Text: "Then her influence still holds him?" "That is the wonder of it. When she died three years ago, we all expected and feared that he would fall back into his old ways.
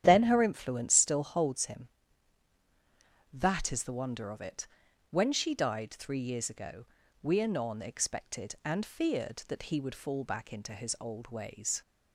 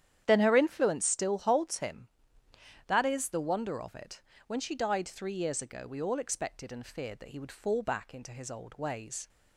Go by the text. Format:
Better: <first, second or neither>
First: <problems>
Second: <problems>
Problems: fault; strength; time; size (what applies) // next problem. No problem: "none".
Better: second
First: starts louder than the rest; strong; until 1.0 s; 10 dB // says "anon" for "all"; at 7.4 s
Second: starts louder than the rest; strong; until 1.2 s; 10 dB